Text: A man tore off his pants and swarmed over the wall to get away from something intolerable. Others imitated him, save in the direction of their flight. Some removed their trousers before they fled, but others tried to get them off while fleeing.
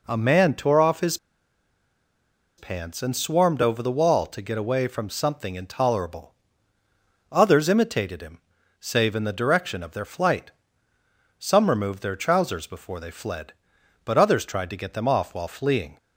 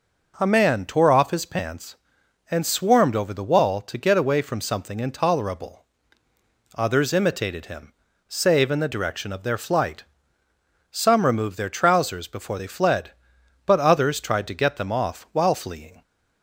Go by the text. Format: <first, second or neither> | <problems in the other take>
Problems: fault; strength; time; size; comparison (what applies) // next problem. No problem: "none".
second | pauses between "his" and "pants"; strong; at 1.1 s; 1.4 s long